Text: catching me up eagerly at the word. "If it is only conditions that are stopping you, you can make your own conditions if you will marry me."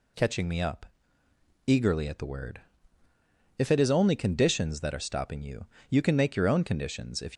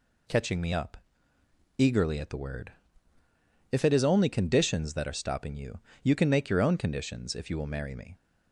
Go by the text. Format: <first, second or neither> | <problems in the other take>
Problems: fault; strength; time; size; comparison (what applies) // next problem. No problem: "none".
second | pauses between "up" and "eagerly"; noticeable; at 0.8 s; 0.80 s long; noticeable in the second // stops before "you will marry me"; at 7.3 s